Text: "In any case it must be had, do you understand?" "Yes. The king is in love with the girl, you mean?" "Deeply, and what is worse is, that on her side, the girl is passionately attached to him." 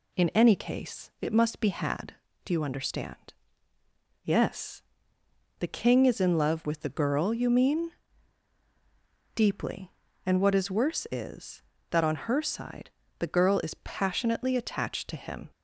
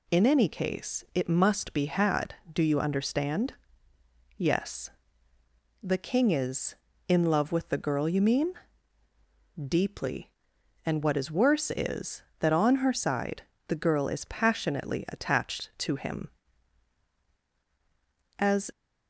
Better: first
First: none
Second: goes on to say "As"; slight; from 18.3 s on; 0.32 s long

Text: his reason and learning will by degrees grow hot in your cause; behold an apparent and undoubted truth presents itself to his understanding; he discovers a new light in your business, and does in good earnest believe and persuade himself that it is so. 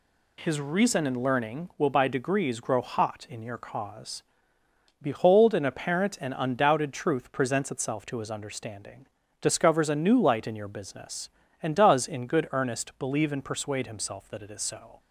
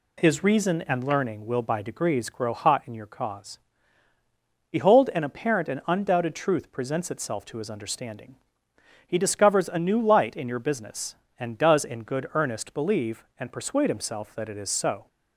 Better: second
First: skips "he"; at 9.2 s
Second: none

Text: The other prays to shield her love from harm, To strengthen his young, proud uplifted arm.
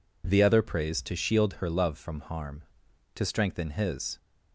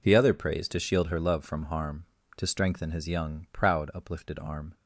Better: second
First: stops before "young proud uplifted arm"; at 4.1 s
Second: none

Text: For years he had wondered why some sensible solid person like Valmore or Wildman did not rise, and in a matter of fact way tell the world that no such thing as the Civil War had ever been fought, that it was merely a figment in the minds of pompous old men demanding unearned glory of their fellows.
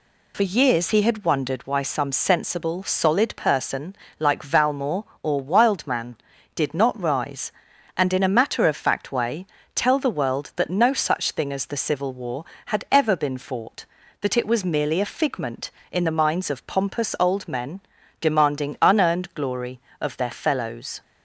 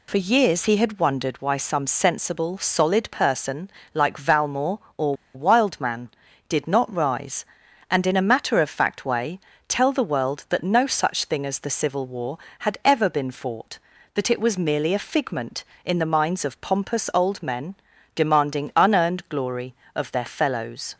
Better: first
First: pauses between "person" and "like"; slight; at 3.9 s; 0.24 s long // pauses between "way" and "tell"; slight; at 9.4 s; 0.28 s long // pauses between "men" and "demanding"; at 17.7 s; 0.40 s long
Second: pauses between "person" and "like"; slight; at 3.6 s; 0.24 s long // pauses between "or" and "Wildman"; slight; at 5.1 s; 0.21 s long // pauses between "way" and "tell"; slight; at 9.3 s; 0.28 s long // pauses between "men" and "demanding"; at 17.7 s; 0.40 s long

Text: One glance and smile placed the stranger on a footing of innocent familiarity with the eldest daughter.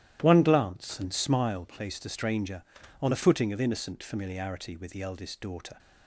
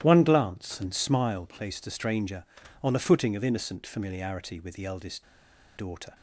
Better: first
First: starts louder than the rest; strong; until 1.2 s; 12.5 dB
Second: starts louder than the rest; strong; until 1.0 s; 12.5 dB // pauses between "eldest" and "daughter"; noticeable; at 5.2 s; 0.53 s long

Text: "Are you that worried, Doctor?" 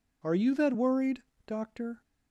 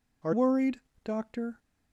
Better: first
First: none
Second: skips "you that"; at 0.3 s

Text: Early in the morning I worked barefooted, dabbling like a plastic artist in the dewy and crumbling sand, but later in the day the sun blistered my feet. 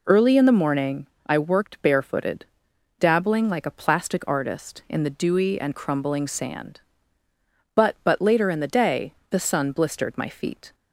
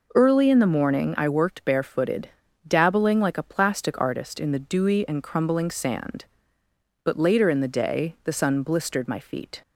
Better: second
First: pauses between "morning" and "I"; slight; at 1.0 s; 0.18 s long // says "but" twice; at 8.0 s // pauses between "day" and "the"; slight; at 9.1 s; 0.16 s long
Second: none

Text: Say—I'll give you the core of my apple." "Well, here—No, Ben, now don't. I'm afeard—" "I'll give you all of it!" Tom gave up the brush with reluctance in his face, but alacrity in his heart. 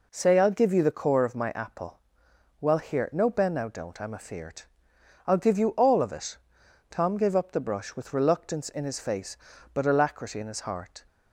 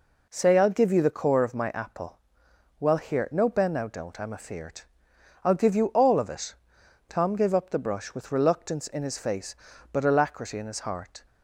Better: neither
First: none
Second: none

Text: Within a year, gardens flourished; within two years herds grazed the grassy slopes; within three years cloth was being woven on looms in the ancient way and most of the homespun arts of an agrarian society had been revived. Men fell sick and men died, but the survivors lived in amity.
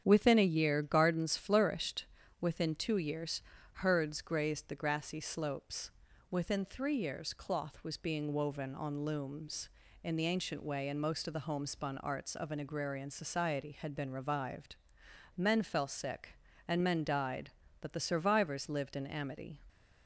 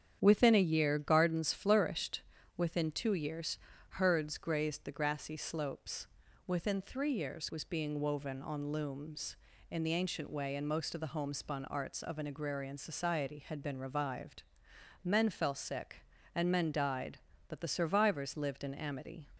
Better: first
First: starts louder than the rest; strong; until 1.0 s; 8.5 dB // pauses between "years" and "herds"; slight; at 3.4 s; 0.36 s long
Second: starts louder than the rest; strong; until 1.2 s; 8.5 dB // pauses between "years" and "herds"; slight; at 3.5 s; 0.36 s long // skips "cloth"; at 7.4 s

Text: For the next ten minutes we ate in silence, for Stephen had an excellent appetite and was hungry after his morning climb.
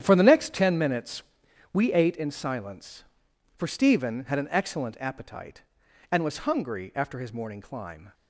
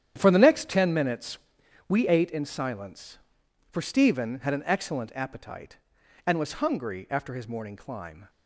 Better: neither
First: starts louder than the rest; strong; until 1.0 s; 9.5 dB // pauses between "minutes" and "we"; noticeable; at 1.2 s; 0.52 s long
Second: starts louder than the rest; strong; until 1.1 s; 9.5 dB // pauses between "minutes" and "we"; noticeable; at 1.3 s; 0.52 s long

